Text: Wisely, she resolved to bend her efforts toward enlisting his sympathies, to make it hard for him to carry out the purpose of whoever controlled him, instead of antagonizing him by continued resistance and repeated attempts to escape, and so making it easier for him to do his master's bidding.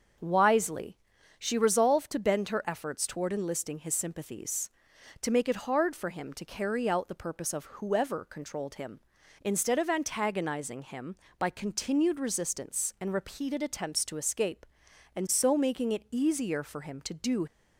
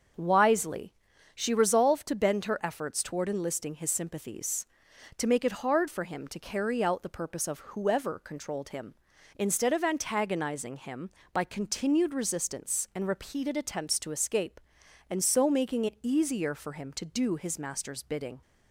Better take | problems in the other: second | starts louder than the rest; until 1.6 s; 6.5 dB; also in the second // stops before "his master's bidding"; at 17.4 s

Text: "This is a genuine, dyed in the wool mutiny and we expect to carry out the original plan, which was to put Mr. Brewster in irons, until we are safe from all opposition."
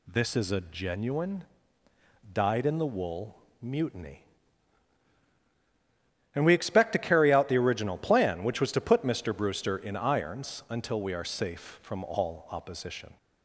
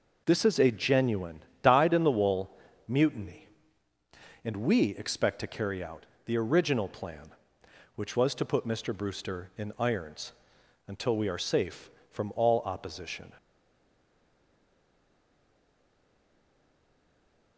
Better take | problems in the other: first | pauses between "wool" and "mutiny"; slight; at 2.4 s; 0.36 s long; slight in the first // pauses between "out" and "the"; slight; at 6.0 s; 0.22 s long // stays silent after the last word; strong; from 13.3 s on; 4.2 s long

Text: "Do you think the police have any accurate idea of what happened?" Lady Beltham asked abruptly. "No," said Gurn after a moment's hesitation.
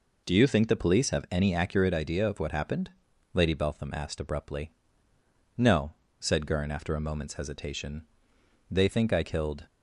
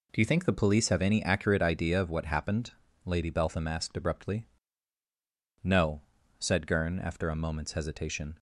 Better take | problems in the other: second | goes on to say "They think I killed"; noticeable; from 8.6 s on; 0.96 s long

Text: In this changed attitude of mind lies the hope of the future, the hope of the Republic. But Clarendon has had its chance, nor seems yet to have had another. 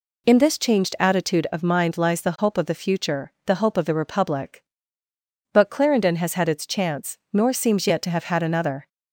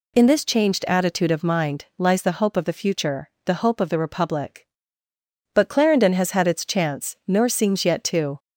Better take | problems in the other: first | stops before "have had another"; at 8.3 s

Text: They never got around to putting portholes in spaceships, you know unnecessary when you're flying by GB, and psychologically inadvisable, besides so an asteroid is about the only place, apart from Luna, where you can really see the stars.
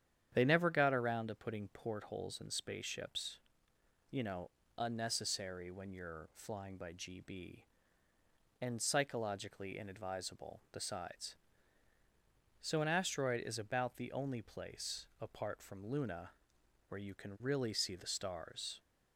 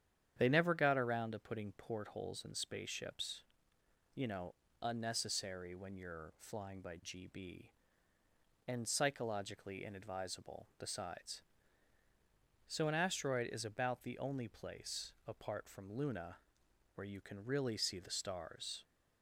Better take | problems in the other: neither | starts louder than the rest; strong; the same in both // pauses between "know" and "unnecessary"; slight; the same in both

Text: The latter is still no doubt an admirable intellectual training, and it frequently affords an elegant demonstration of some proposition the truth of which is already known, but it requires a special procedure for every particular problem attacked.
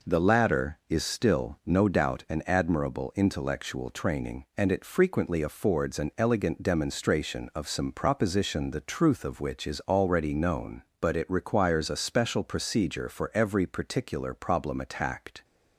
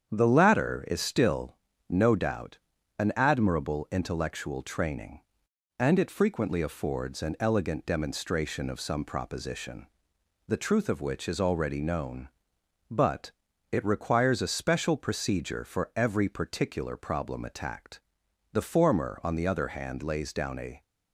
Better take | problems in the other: first | starts louder than the rest; strong; until 1.1 s; 8 dB // pauses between "still" and "no"; slight; at 1.5 s; 0.32 s long // pauses between "doubt" and "an"; at 2.5 s; 0.42 s long // pauses between "proposition" and "the"; noticeable; at 9.8 s; 0.60 s long // pauses between "but" and "it"; at 13.3 s; 0.38 s long // goes on to say "The former on the other hand lays down a"; strong; from 18.5 s on; 2.3 s long

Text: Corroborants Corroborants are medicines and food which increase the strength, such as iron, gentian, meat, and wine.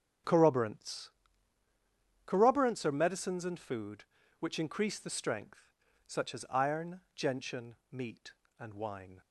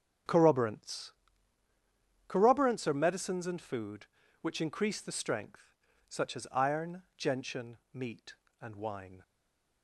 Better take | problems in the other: first | starts louder than the rest; strong; until 2.4 s; 7.5 dB; strong in the first // pauses between "Corroborants" and "Corroborants"; at 1.1 s; 1.1 s long; also in the first // stays silent after the last word; slight; from 9.2 s on; 0.6 s long

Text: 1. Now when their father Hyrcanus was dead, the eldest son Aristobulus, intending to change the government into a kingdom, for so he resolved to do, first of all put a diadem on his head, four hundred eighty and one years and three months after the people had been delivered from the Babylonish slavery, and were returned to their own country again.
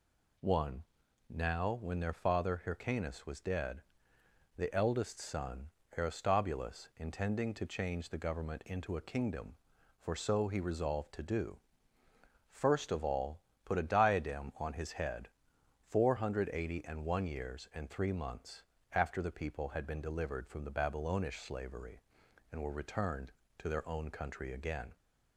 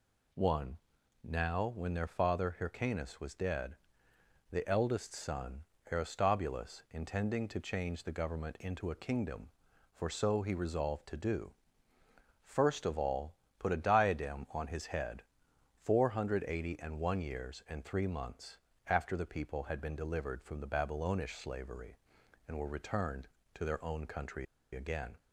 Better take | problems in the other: first | pauses between "son" and "Aristobulus"; slight; at 5.6 s; 0.28 s long; slight in the first // pauses between "all" and "put"; slight; at 13.3 s; 0.26 s long; slight in the first // pauses between "months" and "after"; slight; at 18.5 s; 0.32 s long; slight in the first // pauses between "country" and "again"; slight; at 24.4 s; 0.29 s long

